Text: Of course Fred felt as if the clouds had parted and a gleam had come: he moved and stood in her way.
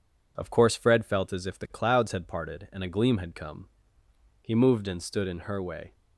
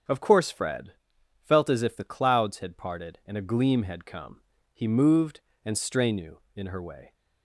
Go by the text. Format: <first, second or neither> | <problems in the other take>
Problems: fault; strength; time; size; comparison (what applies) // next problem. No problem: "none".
first | starts louder than the rest; strong; until 1.6 s; 8 dB // pauses between "Fred" and "felt"; noticeable; at 0.9 s; 0.52 s long // says "strenu" for "stood"; at 5.7 s